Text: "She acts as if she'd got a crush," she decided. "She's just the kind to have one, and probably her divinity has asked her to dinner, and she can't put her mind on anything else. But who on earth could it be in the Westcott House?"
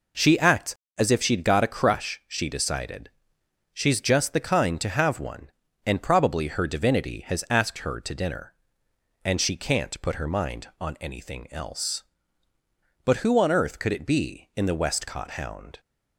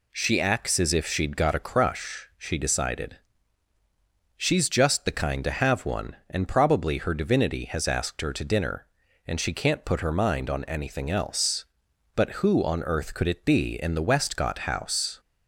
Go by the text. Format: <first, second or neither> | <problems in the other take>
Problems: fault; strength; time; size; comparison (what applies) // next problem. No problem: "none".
second | says "Hound" for "House"; at 15.3 s